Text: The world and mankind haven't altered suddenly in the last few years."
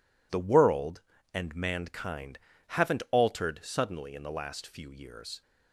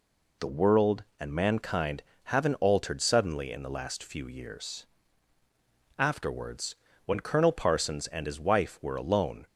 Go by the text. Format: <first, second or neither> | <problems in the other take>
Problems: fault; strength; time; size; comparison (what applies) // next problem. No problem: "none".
first | pauses between "mankind" and "haven't"; slight; at 2.0 s; 0.22 s long; slight in the first // goes on to say "Afterwards when Colonel Parsons and his wife were alone"; strong; from 5.9 s on; 3.4 s long